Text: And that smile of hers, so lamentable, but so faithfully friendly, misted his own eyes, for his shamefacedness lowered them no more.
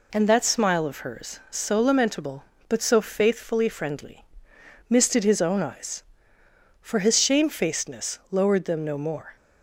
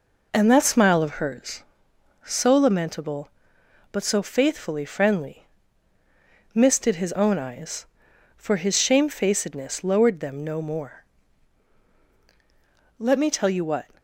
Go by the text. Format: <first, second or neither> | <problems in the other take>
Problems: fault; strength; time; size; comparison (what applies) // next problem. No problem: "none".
first | goes on to say "Let me tell you what"; noticeable; from 12.9 s on; 0.90 s long